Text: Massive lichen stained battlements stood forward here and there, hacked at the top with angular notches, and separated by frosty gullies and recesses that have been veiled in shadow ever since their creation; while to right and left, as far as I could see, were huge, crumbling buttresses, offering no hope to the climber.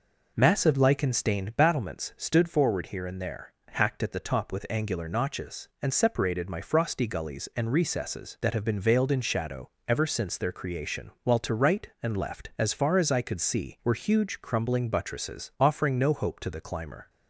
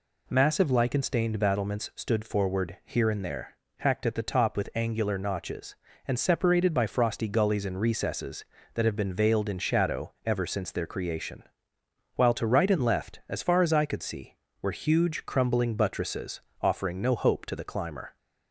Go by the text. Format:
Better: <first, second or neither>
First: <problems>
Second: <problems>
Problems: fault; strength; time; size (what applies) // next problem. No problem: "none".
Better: second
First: says "my" for "by"; at 6.4 s // pauses between "shadow" and "ever"; slight; at 9.6 s; 0.18 s long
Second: none